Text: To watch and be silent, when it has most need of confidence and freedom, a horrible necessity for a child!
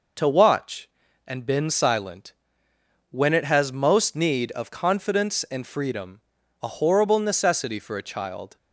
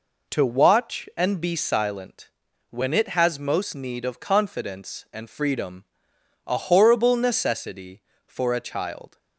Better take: second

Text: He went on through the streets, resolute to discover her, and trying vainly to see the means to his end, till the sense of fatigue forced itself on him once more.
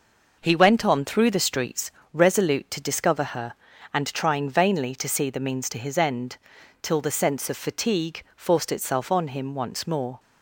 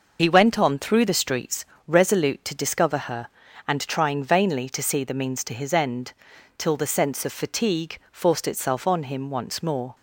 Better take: first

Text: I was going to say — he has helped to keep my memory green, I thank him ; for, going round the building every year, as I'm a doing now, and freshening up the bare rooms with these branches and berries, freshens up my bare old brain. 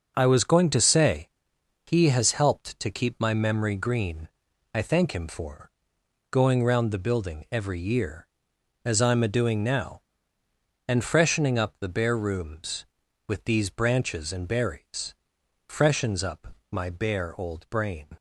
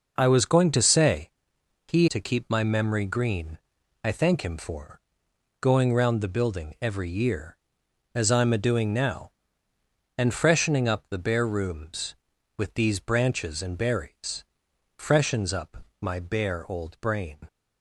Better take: first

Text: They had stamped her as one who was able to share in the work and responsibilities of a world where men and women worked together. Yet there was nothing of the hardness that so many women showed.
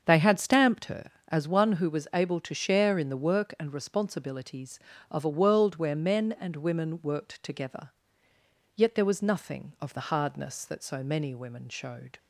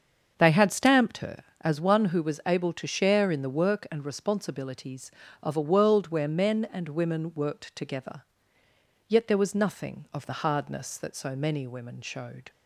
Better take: neither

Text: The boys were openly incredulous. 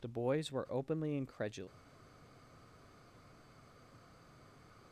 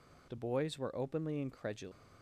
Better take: second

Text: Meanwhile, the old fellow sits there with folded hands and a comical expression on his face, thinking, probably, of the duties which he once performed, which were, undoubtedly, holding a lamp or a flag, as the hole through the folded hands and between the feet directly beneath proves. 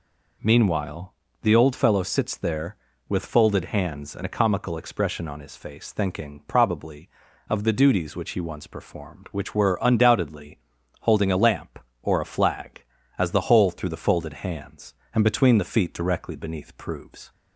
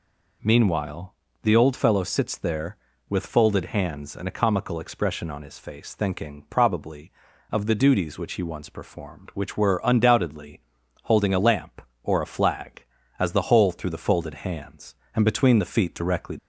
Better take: first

